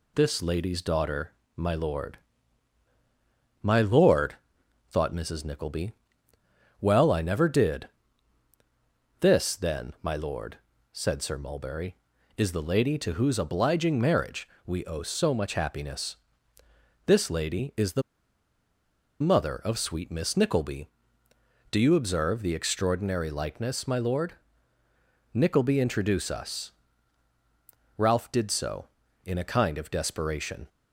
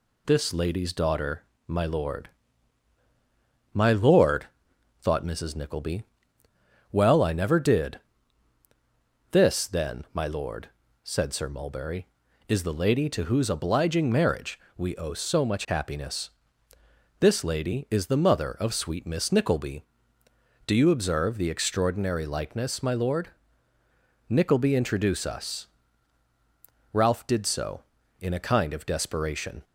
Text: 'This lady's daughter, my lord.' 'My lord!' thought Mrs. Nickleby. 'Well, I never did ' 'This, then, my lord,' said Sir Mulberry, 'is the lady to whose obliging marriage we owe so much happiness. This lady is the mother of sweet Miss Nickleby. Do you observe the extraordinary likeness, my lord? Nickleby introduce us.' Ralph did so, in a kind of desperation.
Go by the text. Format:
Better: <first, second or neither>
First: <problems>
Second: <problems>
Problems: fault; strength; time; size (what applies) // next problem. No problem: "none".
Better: second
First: pauses between "marriage" and "we"; slight; at 14.4 s; 0.20 s long // pauses between "the" and "mother"; at 18.0 s; 1.2 s long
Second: pauses between "marriage" and "we"; slight; at 14.5 s; 0.20 s long